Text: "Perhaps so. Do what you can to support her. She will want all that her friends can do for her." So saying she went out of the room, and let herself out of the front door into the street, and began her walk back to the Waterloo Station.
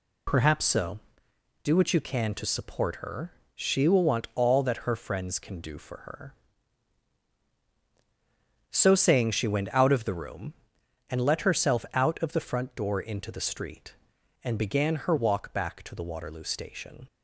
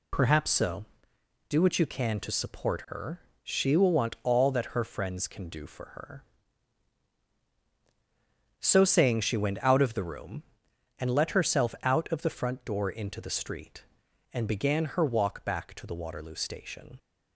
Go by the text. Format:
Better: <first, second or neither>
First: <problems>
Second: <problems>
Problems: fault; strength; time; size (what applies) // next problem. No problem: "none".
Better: neither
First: none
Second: none